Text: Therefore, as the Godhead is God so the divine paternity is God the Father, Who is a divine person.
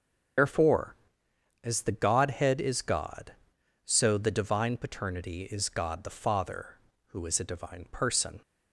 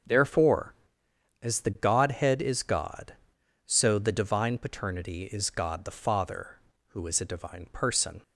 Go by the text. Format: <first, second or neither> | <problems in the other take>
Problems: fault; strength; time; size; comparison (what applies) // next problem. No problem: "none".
second | loses the start of "Therefore"; at 0.3 s; 115 ms // starts louder than the rest; until 2.0 s; 6.5 dB; also in the second